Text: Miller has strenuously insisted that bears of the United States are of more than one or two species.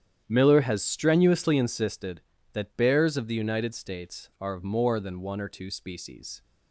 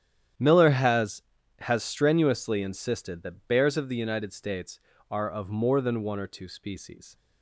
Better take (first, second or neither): first